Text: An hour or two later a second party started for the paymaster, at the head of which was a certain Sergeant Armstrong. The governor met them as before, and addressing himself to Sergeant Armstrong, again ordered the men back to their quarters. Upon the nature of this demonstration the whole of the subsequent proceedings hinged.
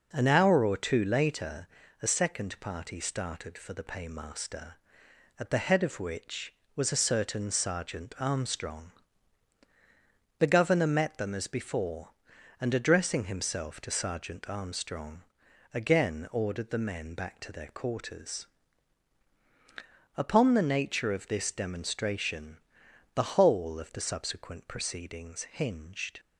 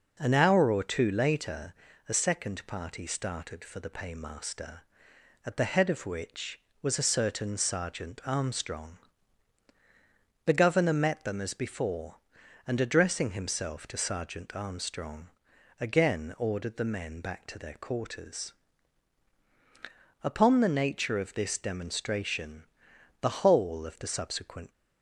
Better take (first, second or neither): first